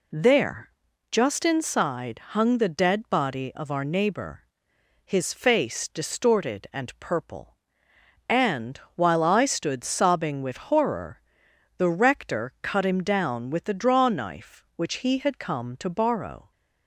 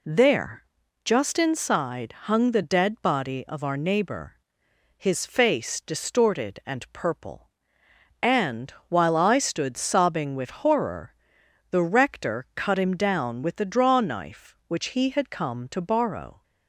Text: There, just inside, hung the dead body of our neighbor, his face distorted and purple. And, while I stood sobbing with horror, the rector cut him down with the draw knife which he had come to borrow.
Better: neither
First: none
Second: none

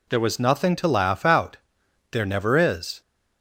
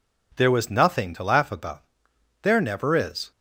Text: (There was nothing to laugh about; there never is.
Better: second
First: says "out" for "about"; at 1.2 s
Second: none

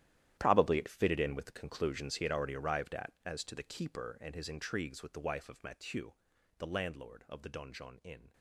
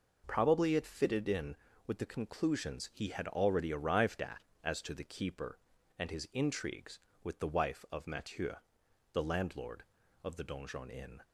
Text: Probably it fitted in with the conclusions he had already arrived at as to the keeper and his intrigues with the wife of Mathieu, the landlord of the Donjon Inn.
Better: second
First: gets quieter; strong; throughout; 15 dB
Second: none

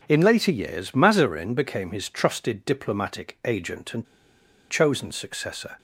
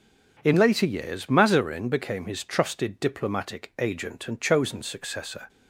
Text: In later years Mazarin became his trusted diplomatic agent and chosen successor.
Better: second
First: pauses between "and" and "chosen"; noticeable; at 4.0 s; 0.65 s long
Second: none

